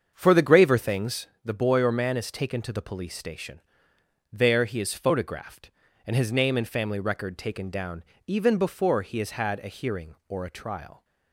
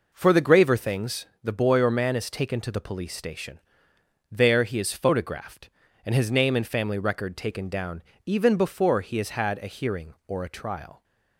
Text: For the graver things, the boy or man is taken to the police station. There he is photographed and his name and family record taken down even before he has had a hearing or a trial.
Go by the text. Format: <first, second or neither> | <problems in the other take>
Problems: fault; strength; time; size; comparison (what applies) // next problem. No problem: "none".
second | starts louder than the rest; strong; until 1.2 s; 7 dB // pauses between "down" and "even"; slight; at 8.0 s; 0.22 s long; slight in the second